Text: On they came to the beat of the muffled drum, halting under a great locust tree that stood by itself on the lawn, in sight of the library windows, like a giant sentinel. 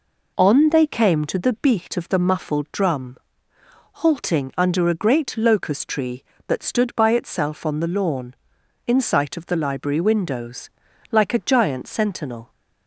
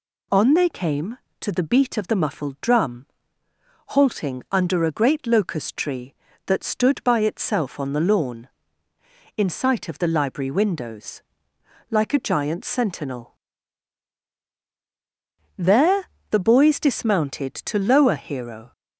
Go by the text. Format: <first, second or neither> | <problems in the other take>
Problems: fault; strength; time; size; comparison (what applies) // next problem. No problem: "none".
first | goes on to say "There the boys dismounted to lower Hero"; strong; from 15.5 s on; 3.1 s long